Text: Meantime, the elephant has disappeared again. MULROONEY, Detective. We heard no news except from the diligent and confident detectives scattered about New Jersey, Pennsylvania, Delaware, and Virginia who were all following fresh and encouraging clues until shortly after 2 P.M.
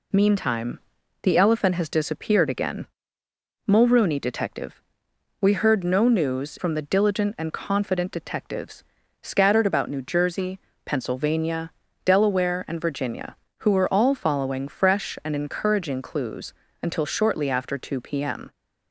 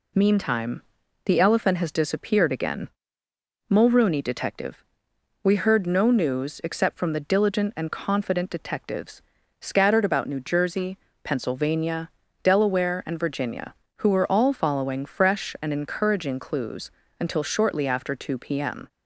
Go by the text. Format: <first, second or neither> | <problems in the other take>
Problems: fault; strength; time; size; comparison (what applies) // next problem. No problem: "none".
second | skips "except"; at 6.5 s // pauses between "detectives" and "scattered"; slight; at 8.8 s; 0.36 s long; slight in the second // pauses between "clues" and "until"; slight; at 16.5 s; 0.30 s long; slight in the second